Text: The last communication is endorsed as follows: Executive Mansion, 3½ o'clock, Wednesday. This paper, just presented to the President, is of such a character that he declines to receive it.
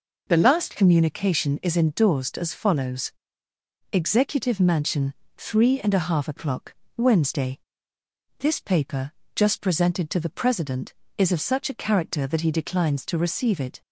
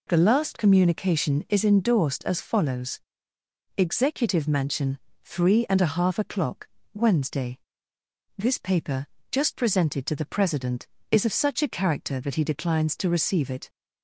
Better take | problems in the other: neither | none

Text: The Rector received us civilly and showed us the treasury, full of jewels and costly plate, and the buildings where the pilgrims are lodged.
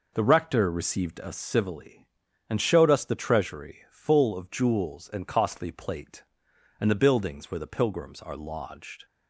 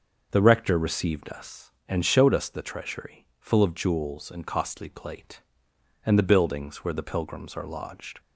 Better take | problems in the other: first | starts louder than the rest; until 1.3 s; 6 dB // skips "civilly"; at 1.7 s

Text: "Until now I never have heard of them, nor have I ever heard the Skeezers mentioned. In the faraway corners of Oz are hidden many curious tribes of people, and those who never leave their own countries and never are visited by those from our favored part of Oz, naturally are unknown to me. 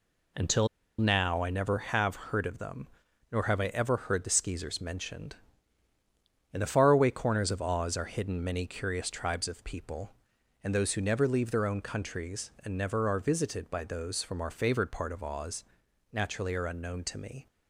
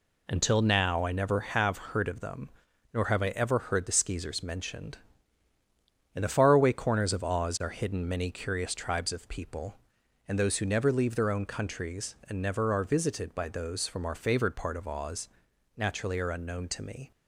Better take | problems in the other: second | pauses between "Until" and "now"; slight; at 0.6 s; 0.30 s long

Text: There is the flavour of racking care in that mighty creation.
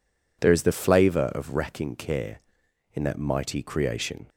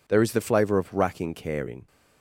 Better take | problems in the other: first | stops before "that mighty creation"; at 1.8 s

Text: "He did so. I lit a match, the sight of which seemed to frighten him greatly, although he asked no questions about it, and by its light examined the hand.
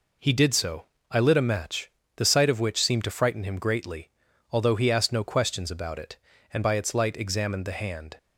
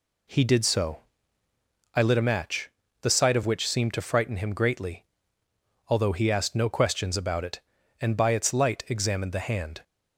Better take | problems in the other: neither | none

